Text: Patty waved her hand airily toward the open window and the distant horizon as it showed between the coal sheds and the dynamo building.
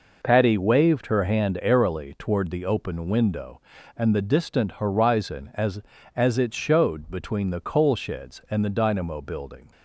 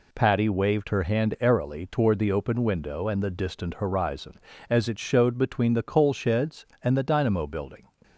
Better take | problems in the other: second | says "as" twice; at 6.1 s

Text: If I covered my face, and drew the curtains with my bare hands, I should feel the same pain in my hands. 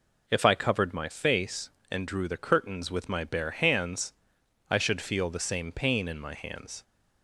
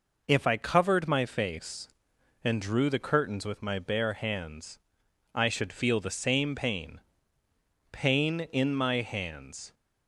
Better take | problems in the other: first | says "pain" twice; at 7.9 s

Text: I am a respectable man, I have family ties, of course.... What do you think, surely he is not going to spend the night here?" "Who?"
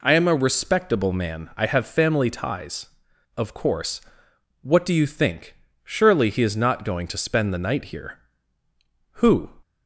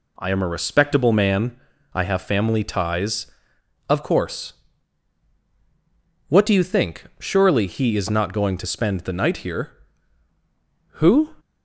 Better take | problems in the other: neither | none

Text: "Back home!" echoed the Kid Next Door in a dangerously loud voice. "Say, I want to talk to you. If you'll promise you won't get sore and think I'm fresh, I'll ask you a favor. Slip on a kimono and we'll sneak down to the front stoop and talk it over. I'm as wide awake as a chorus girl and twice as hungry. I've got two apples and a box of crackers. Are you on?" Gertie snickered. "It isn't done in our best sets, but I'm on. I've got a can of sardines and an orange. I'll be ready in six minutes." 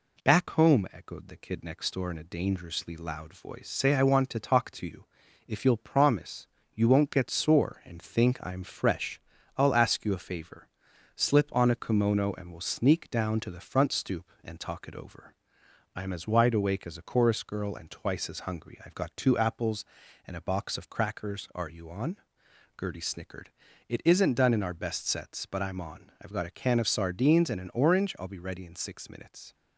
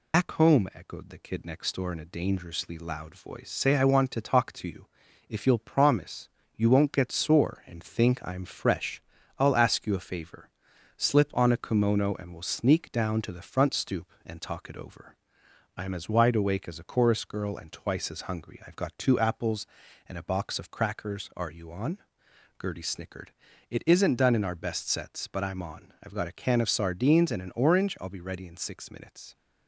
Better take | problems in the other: first | loses the start of "Back"; at 0.1 s; 140 ms // pauses between "promise" and "you"; slight; at 6.2 s; 0.26 s long; slight in the first

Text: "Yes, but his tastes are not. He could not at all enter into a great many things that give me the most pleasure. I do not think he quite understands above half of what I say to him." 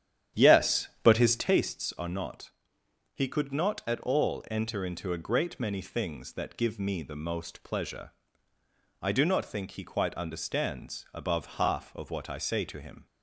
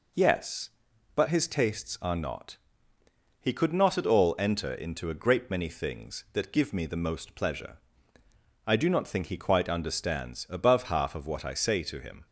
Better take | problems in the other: second | starts louder than the rest; strong; until 1.6 s; 10 dB

